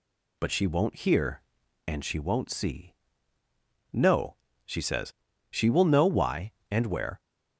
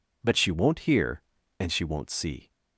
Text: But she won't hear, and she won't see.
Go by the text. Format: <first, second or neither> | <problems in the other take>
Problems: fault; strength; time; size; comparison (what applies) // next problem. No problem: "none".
second | goes on to say "No she says she will know why and where"; strong; from 3.9 s on; 3.2 s long